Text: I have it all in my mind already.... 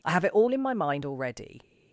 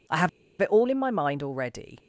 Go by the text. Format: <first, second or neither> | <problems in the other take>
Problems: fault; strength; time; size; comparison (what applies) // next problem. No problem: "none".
first | pauses between "have" and "it"; slight; at 0.2 s; 0.30 s long